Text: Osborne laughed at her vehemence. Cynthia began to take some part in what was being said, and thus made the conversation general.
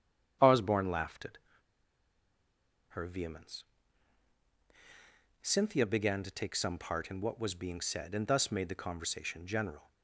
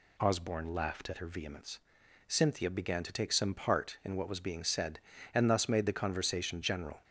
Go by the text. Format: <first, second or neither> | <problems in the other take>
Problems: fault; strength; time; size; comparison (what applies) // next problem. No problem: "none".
second | starts louder than the rest; strong; until 2.9 s; 9 dB // pauses between "at" and "her"; strong; at 1.3 s; 1.5 s long